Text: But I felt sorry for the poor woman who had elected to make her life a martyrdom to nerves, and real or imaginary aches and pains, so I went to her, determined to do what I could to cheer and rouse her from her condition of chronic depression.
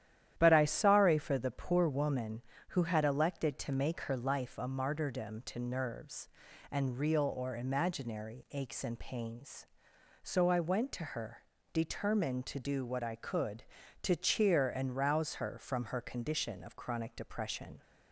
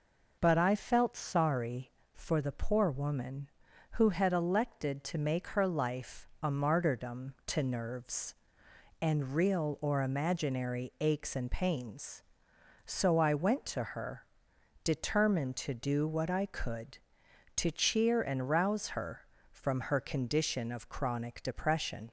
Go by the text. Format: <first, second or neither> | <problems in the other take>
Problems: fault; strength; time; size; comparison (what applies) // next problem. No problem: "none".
second | starts louder than the rest; strong; until 1.3 s; 11 dB // skips "felt"; at 0.6 s